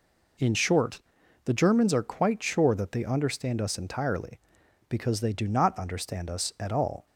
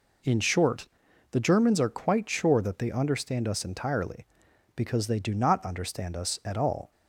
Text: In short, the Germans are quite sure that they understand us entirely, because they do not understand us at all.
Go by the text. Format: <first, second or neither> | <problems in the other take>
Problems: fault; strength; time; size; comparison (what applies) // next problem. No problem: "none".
neither | none